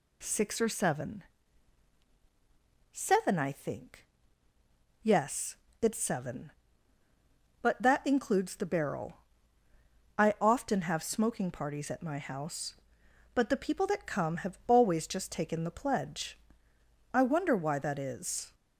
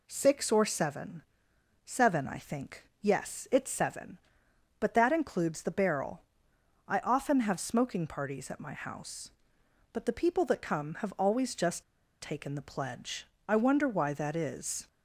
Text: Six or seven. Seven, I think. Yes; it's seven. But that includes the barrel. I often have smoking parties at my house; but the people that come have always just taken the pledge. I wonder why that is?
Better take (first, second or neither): first